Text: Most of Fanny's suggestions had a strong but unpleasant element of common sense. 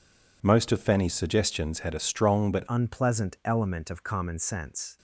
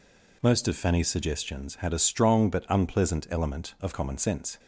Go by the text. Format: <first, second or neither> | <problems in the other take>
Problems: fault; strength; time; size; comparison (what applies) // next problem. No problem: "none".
second | changes voice at "unpleasant"; from 2.6 s on; 2.3 s long